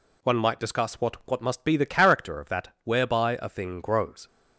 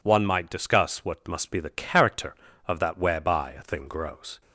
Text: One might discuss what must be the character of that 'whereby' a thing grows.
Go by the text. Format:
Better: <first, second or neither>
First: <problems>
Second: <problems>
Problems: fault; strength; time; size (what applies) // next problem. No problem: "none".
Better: second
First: says "what" twice; at 1.2 s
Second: none